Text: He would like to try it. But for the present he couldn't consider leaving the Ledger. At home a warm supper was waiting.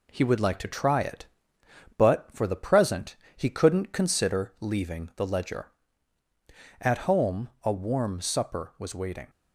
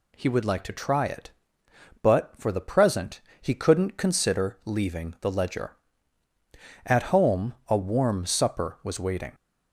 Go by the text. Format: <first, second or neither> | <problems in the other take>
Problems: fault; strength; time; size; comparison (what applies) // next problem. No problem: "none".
second | gets quieter; slight; throughout; 3 dB // pauses between "present" and "he"; slight; at 3.1 s; 0.22 s long; slight in the second